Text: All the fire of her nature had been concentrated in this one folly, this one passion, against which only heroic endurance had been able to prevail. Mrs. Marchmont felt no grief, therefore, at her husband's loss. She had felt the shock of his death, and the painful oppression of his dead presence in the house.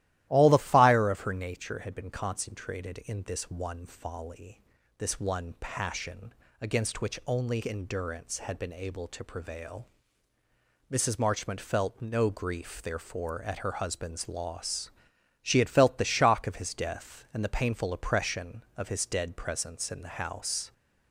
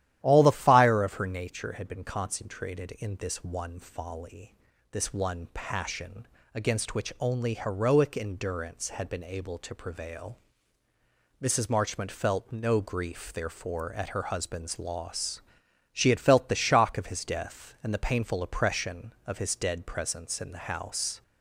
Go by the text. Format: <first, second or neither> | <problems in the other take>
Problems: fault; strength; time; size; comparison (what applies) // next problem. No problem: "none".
second | starts louder than the rest; strong; until 1.3 s; 14.5 dB; strong in the second // skips "heroic"; at 7.6 s